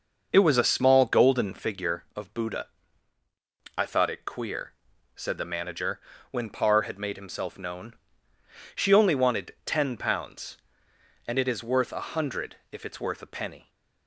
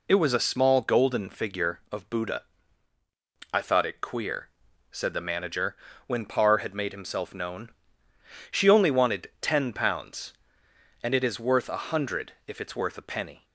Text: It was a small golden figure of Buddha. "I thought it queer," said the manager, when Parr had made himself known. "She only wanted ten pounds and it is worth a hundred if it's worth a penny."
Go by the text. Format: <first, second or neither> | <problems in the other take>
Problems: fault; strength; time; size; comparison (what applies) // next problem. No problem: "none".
second | starts louder than the rest; noticeable; until 1.7 s; 6 dB // pauses between "hundred" and "if"; slight; at 12.5 s; 0.16 s long